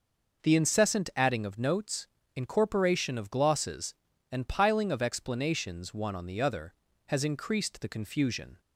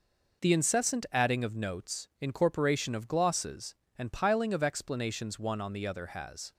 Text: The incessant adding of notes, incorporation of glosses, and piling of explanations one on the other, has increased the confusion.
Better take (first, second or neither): first